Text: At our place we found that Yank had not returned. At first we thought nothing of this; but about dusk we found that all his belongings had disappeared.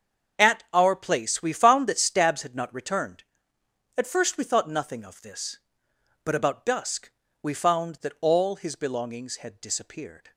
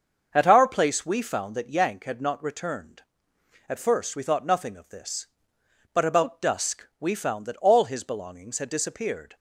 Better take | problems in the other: second | starts louder than the rest; until 1.4 s; 7 dB; also in the second // says "Stabs" for "Yank"; at 1.9 s // pauses between "dusk" and "we"; slight; at 7.1 s; 0.28 s long

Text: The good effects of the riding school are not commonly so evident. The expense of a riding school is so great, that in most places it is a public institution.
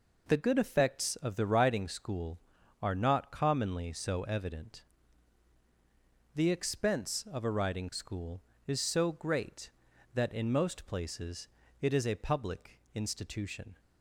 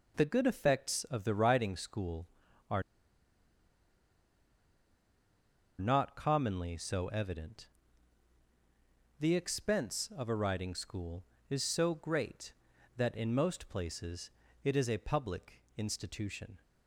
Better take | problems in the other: first | pauses between "are" and "not"; strong; at 2.8 s; 2.9 s long // pauses between "places" and "it"; slight; at 14.2 s; 0.34 s long; slight in the first

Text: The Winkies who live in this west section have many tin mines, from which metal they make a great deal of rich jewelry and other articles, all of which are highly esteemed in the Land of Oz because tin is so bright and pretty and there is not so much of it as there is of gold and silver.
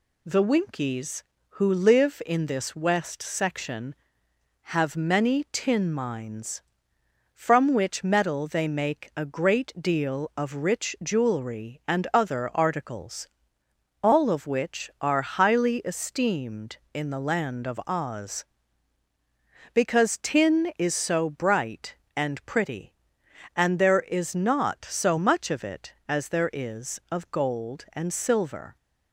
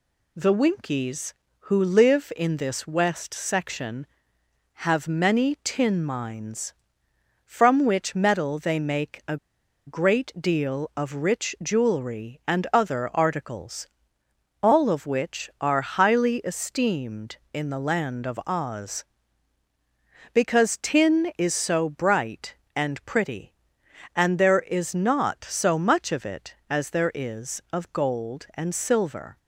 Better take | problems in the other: first | pauses between "a" and "great"; noticeable; at 9.3 s; 0.51 s long

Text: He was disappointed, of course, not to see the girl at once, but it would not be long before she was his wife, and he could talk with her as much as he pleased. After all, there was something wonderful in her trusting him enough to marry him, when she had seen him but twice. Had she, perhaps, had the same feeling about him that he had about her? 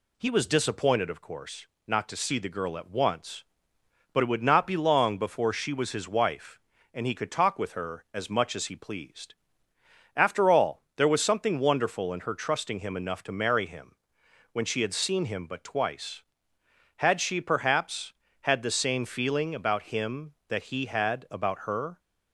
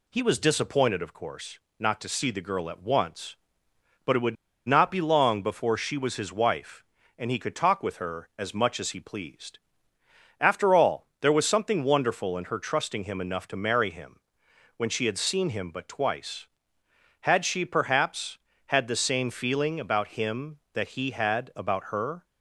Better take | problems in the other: first | pauses between "would" and "not"; slight; at 4.3 s; 0.32 s long

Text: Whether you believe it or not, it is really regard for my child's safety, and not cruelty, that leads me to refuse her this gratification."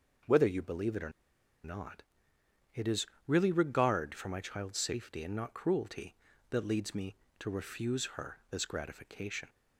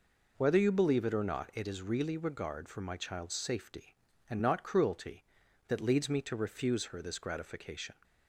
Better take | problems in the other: second | pauses between "or" and "not"; noticeable; at 1.0 s; 0.54 s long // pauses between "is" and "really"; slight; at 3.0 s; 0.20 s long

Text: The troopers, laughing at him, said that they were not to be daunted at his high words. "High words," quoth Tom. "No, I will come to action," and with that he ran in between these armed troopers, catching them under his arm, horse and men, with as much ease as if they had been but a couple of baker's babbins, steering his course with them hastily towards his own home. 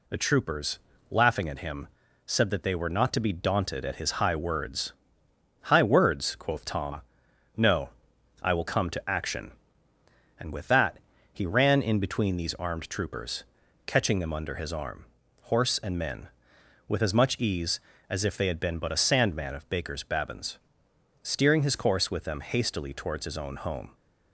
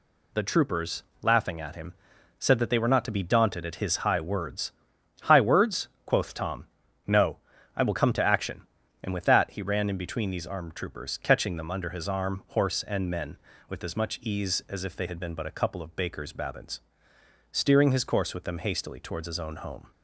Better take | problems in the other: second | pauses between "that" and "he"; slight; at 10.9 s; 0.34 s long // says "sandman" for "couple"; at 18.9 s

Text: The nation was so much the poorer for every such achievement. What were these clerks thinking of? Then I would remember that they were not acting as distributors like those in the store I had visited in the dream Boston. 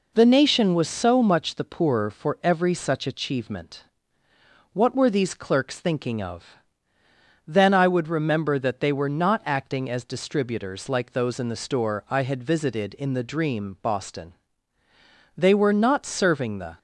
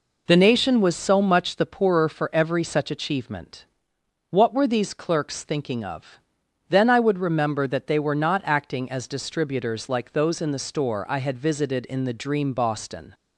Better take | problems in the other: second | goes on to say "They were not serving the"; from 15.3 s on; 1.4 s long

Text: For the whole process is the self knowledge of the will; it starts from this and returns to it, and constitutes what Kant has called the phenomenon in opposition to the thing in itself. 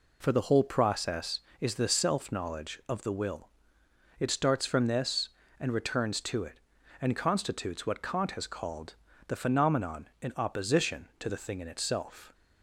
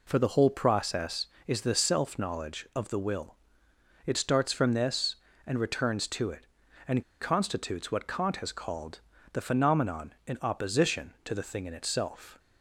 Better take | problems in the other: first | pauses between "and" and "constitutes"; slight; at 7.0 s; 0.17 s long // pauses between "called" and "the"; slight; at 9.0 s; 0.32 s long; slight in the first

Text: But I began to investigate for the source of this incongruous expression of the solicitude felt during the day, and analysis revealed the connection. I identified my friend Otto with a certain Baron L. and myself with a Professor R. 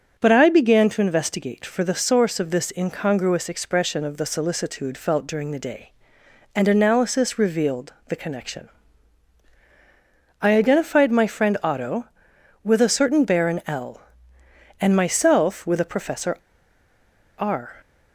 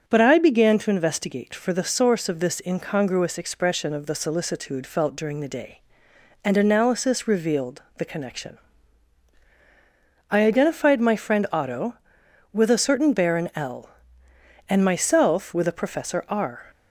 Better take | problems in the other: second | starts louder than the rest; until 1.1 s; 6.5 dB; also in the second // pauses between "revealed" and "the"; slight; at 7.9 s; 0.16 s long; slight in the second // pauses between "Professor" and "R"; at 16.3 s; 1.0 s long

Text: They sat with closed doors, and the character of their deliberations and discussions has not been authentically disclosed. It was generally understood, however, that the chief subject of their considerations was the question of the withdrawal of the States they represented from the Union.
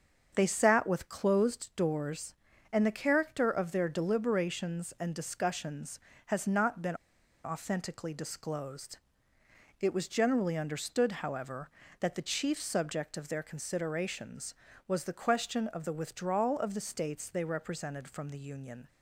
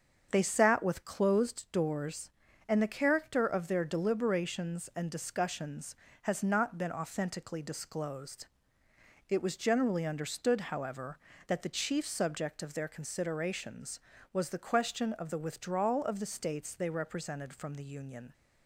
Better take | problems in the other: second | starts louder than the rest; until 1.3 s; 7 dB; also in the second // pauses between "been" and "authentically"; noticeable; at 6.9 s; 0.48 s long

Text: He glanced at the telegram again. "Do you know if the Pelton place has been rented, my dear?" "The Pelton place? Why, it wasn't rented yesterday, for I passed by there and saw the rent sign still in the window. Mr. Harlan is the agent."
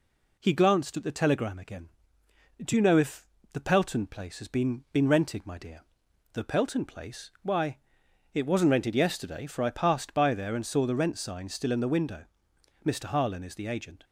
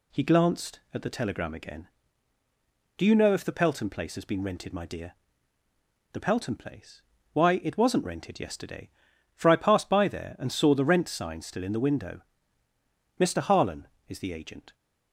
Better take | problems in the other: second | pauses between "if" and "the"; slight; at 3.2 s; 0.28 s long // says "been" twice; at 4.9 s

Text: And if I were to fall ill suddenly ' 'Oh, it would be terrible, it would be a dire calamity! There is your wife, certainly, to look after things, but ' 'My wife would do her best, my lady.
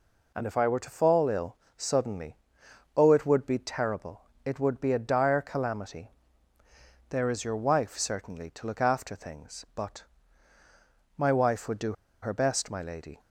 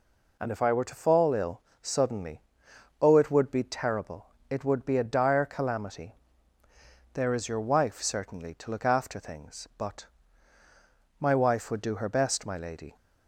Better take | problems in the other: second | pauses between "ill" and "suddenly"; slight; at 1.5 s; 0.20 s long; slight in the second // pauses between "do" and "her"; slight; at 11.9 s; 0.29 s long

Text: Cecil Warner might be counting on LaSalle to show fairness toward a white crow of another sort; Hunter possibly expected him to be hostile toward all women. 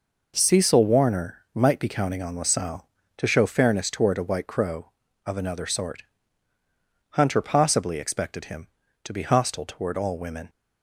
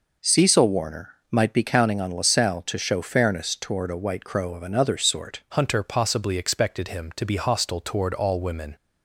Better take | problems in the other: first | pauses between "Warner" and "might"; slight; at 1.1 s; 0.16 s long // changes voice at "Hunter"; from 5.5 s on; 3.2 s long

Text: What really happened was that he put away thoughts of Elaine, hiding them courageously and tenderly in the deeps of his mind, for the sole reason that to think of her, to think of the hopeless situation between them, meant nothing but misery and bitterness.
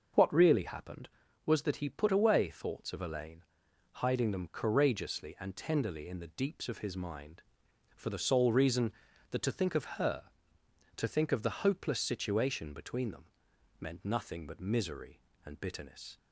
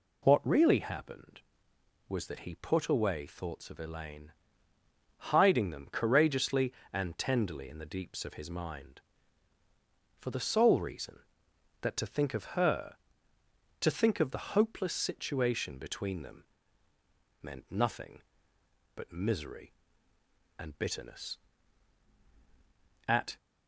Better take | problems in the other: first | goes on to say "At"; slight; from 23.0 s on; 0.30 s long

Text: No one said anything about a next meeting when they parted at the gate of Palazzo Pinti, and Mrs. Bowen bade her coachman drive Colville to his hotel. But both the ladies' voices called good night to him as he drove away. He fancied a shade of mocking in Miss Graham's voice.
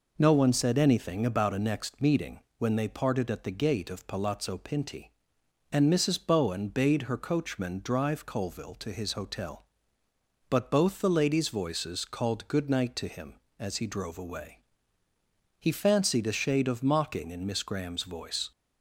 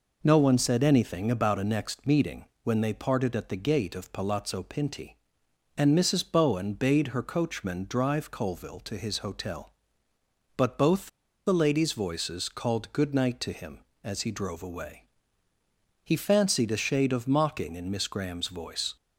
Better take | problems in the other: first | pauses between "meeting" and "when"; slight; at 2.4 s; 0.20 s long; slight in the first // pauses between "both" and "the"; at 11.0 s; 0.39 s long

